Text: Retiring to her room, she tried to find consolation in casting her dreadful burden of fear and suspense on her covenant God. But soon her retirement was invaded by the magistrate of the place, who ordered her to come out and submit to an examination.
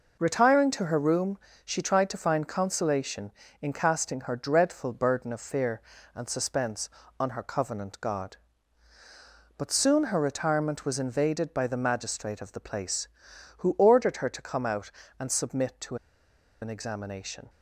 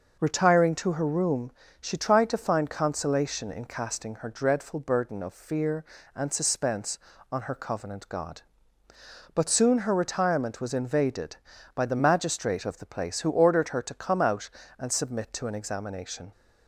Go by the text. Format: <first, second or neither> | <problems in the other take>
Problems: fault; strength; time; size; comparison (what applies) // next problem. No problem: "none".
second | pauses between "to" and "an"; noticeable; at 15.9 s; 0.66 s long